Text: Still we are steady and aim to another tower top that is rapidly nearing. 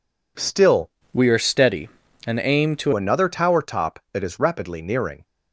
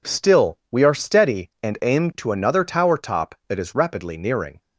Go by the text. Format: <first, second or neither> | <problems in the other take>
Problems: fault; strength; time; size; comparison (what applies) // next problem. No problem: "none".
second | changes voice from "we" to "to"; from 1.1 to 2.9 s; 1.8 s long